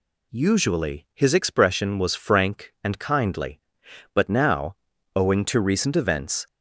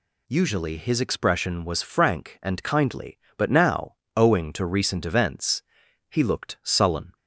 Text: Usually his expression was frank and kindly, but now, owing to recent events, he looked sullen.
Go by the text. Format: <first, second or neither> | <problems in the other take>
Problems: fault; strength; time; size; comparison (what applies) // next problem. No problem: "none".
second | stops before "he looked sullen"; at 6.4 s